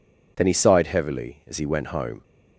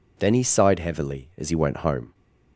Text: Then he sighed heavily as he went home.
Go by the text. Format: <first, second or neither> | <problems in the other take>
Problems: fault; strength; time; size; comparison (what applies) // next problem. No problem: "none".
neither | none